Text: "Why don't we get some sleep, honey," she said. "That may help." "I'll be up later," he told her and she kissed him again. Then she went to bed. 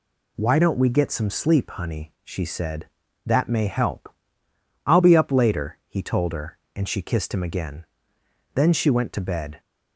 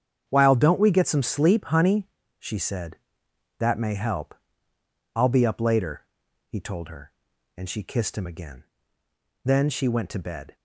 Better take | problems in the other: first | starts louder than the rest; strong; until 1.3 s; 8 dB // says "While" for "Why"; at 0.2 s

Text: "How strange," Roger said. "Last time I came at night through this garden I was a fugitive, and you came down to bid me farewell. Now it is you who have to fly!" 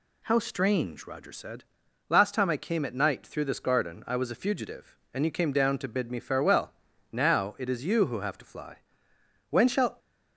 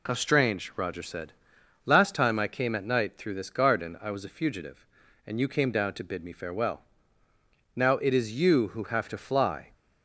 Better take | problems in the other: second | goes on to say "When shall"; slight; from 9.5 s on; 0.48 s long

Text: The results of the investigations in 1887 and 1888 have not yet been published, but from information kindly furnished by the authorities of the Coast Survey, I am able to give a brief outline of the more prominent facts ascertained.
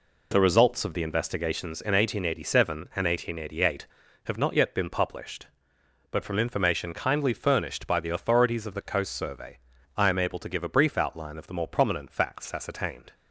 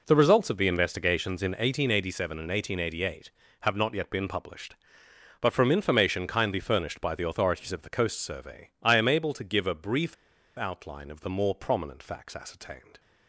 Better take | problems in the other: first | pauses between "brief" and "outline"; at 10.1 s; 0.42 s long

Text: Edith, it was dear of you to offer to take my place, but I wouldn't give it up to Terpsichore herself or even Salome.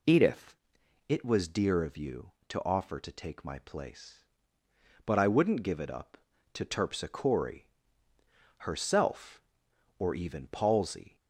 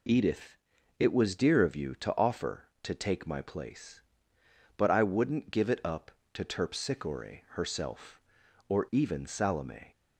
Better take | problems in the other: second | pauses between "Terpsichore" and "herself"; noticeable; at 7.6 s; 0.90 s long // says "Palsy" for "Salome"; at 10.4 s

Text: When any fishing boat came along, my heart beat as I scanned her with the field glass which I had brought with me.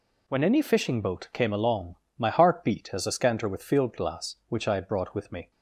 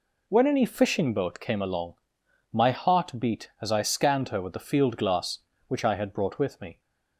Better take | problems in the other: second | skips "the"; at 3.6 s

